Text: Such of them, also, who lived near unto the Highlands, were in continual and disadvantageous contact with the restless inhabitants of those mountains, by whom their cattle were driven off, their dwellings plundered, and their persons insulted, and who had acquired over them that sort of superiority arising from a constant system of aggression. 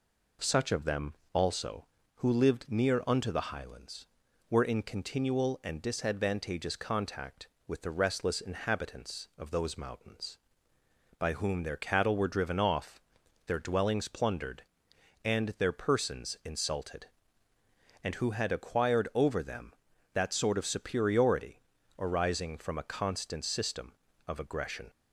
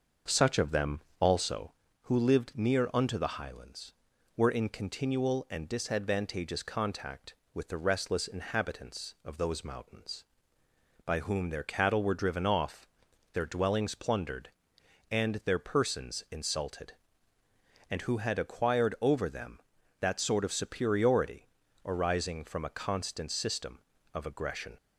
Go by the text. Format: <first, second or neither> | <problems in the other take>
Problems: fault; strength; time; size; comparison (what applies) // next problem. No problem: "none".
first | starts louder than the rest; until 1.8 s; 6.5 dB // pauses between "superiority" and "arising"; at 21.4 s; 0.38 s long; also in the first